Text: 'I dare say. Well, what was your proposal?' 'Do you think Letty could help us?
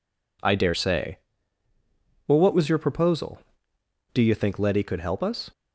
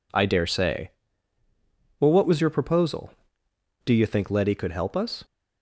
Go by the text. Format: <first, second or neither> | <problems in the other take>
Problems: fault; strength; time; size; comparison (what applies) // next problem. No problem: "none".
neither | none